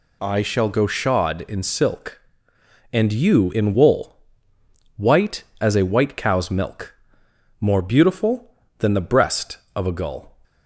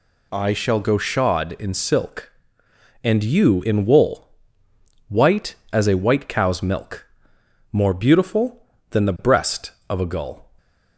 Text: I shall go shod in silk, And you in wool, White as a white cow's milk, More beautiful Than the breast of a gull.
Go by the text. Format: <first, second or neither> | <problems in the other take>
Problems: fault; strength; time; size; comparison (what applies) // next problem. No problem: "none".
neither | none